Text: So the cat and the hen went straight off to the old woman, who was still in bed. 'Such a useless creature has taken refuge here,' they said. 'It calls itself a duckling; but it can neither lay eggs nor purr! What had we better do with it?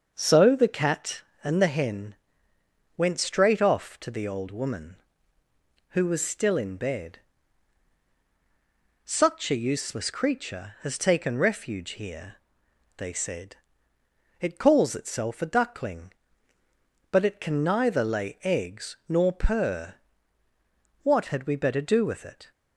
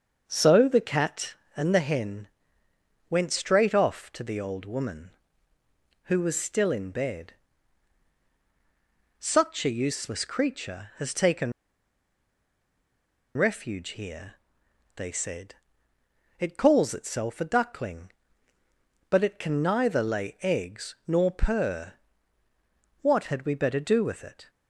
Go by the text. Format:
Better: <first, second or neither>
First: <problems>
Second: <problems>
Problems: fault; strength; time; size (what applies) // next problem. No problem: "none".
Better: first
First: starts louder than the rest; until 1.1 s; 6.5 dB // pauses between "hen" and "went"; noticeable; at 2.1 s; 0.82 s long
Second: starts louder than the rest; until 1.2 s; 6.5 dB // pauses between "hen" and "went"; noticeable; at 2.2 s; 0.82 s long // pauses between "taken" and "refuge"; strong; at 11.5 s; 1.8 s long